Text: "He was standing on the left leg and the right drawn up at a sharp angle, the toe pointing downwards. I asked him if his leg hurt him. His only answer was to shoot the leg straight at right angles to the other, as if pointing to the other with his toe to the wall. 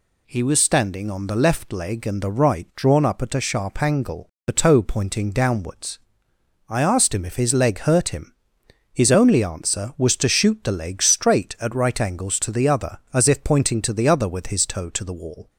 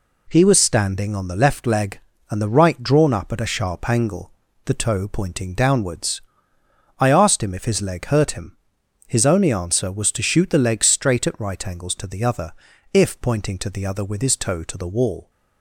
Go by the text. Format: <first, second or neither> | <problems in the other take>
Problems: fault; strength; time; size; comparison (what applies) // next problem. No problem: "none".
first | skips "as"; at 12.7 s